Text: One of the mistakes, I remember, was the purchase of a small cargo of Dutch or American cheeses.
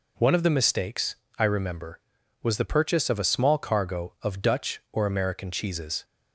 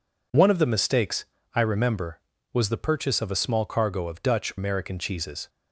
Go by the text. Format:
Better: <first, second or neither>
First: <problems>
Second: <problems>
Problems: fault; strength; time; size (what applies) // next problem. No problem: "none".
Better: first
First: none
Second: skips "or"; at 4.5 s